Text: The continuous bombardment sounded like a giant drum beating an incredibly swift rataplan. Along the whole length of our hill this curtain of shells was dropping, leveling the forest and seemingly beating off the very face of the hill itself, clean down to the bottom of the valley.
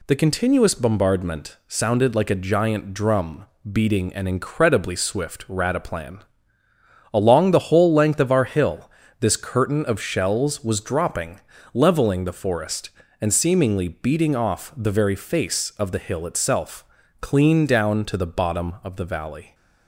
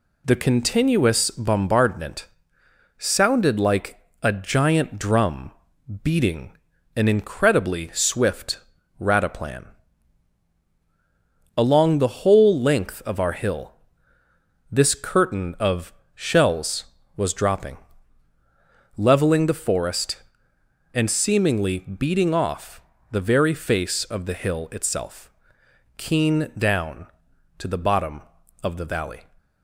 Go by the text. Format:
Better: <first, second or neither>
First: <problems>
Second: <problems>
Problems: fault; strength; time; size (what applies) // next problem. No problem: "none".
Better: first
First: pauses between "drum" and "beating"; slight; at 3.4 s; 0.26 s long // pauses between "hill" and "this"; slight; at 8.8 s; 0.32 s long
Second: pauses between "bombardment" and "sounded"; noticeable; at 2.2 s; 0.72 s long // pauses between "like" and "a"; slight; at 4.0 s; 0.22 s long // pauses between "drum" and "beating"; noticeable; at 5.5 s; 0.50 s long // pauses between "beating" and "an"; at 6.5 s; 0.38 s long // pauses between "swift" and "rataplan"; at 8.5 s; 0.40 s long // pauses between "hill" and "this"; noticeable; at 13.7 s; 0.98 s long // pauses between "of" and "shells"; slight; at 15.9 s; 0.22 s long // pauses between "off" and "the"; slight; at 22.8 s; 0.30 s long // says "keen" for "clean"; at 25.9 s